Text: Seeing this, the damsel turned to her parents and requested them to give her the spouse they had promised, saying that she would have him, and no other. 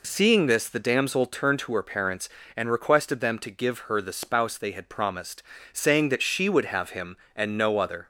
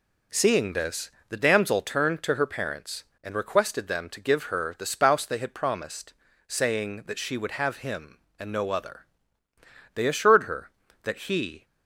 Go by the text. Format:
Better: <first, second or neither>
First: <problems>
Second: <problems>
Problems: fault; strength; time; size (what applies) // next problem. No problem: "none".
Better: first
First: none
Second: goes on to say "They assured her that he"; strong; from 9.9 s on; 1.7 s long